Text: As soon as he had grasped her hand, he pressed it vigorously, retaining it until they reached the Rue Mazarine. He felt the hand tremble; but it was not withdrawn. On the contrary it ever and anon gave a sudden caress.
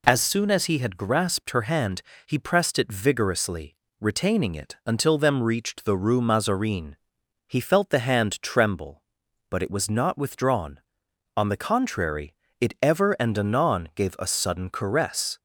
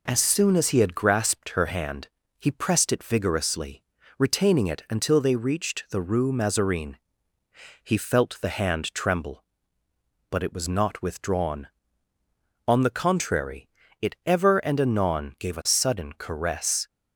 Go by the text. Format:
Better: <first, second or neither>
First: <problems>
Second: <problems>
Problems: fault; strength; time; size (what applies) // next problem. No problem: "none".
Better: second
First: says "them" for "they"; at 5.1 s // pauses between "contrary" and "it"; slight; at 12.3 s; 0.26 s long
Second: pauses between "contrary" and "it"; slight; at 13.6 s; 0.32 s long